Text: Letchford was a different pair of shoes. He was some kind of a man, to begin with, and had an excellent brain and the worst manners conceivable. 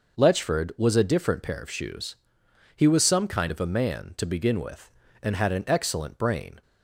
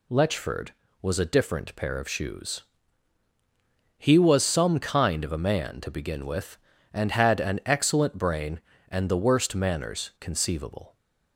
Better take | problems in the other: second | stops before "and the worst manners conceivable"; at 6.6 s

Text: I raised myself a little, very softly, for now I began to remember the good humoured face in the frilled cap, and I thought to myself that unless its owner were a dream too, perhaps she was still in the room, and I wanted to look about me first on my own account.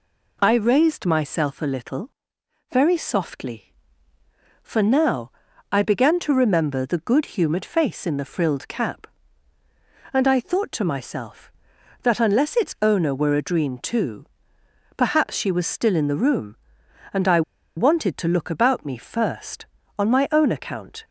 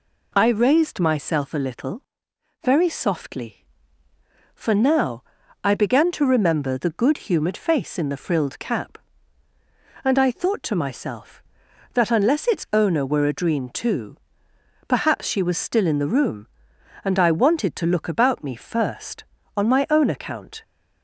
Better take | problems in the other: second | pauses between "now" and "I"; at 5.3 s; 0.38 s long; also in the second // pauses between "I" and "wanted"; slight; at 17.4 s; 0.35 s long

